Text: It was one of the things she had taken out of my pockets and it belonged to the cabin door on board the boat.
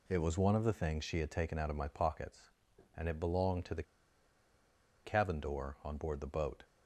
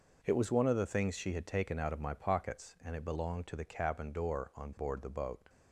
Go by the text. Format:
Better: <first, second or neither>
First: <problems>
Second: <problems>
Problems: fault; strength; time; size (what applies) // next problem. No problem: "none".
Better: second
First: pauses between "the" and "cabin"; at 3.8 s; 1.2 s long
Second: none